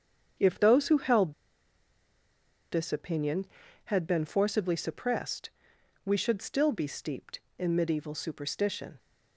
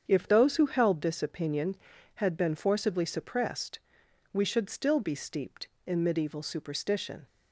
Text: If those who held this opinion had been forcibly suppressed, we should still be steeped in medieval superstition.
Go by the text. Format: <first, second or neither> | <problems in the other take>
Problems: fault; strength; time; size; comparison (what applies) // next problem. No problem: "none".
second | starts louder than the rest; strong; until 2.7 s; 7.5 dB; strong in the second // pauses between "held" and "this"; strong; at 1.3 s; 1.3 s long